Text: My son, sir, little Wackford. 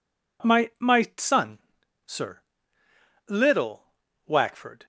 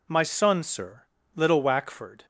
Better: second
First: says "My" twice; at 0.7 s // pauses between "little" and "Wackford"; at 3.8 s; 0.42 s long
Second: none

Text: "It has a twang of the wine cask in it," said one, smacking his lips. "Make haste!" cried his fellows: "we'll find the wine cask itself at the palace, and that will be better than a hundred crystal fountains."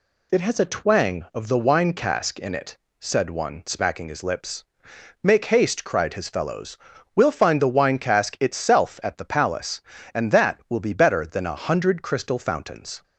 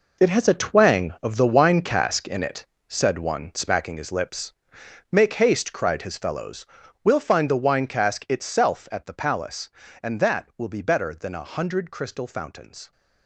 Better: first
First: none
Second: gets quieter; strong; throughout; 12 dB

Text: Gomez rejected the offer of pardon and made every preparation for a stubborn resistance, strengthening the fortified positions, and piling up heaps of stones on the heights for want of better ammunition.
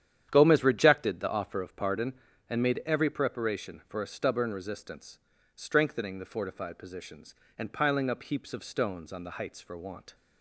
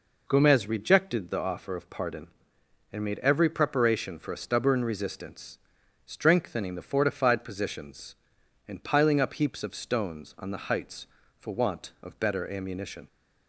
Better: second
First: starts louder than the rest; strong; until 1.3 s; 9.5 dB // stops before "of better ammunition"; at 10.1 s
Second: none

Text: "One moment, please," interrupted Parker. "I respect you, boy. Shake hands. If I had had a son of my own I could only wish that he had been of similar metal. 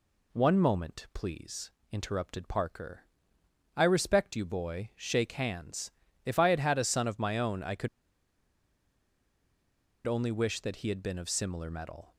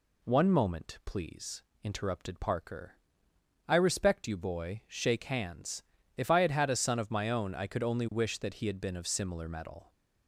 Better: second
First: pauses between "could" and "only"; strong; at 7.8 s; 2.1 s long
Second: none

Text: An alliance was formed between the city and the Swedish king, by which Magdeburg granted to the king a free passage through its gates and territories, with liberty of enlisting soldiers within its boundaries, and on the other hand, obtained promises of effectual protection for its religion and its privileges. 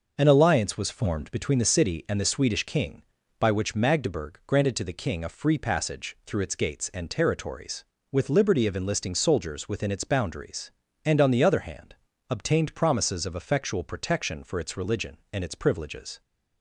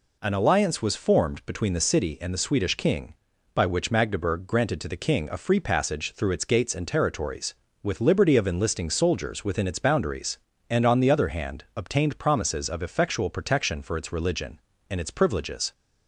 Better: neither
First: none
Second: none

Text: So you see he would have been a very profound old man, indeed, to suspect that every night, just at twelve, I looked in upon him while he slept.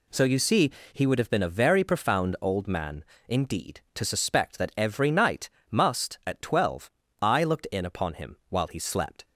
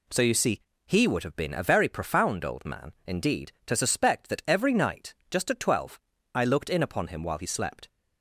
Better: second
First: pauses between "see" and "he"; slight; at 0.6 s; 0.22 s long // says "must" for "just"; at 5.6 s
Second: pauses between "see" and "he"; slight; at 0.5 s; 0.26 s long

